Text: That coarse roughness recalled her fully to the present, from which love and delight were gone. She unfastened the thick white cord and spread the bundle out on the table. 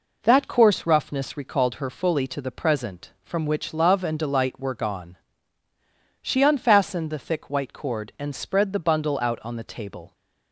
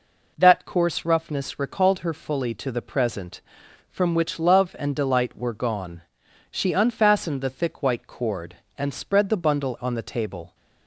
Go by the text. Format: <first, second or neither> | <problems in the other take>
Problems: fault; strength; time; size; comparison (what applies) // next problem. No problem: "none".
first | skips "out"; at 9.7 s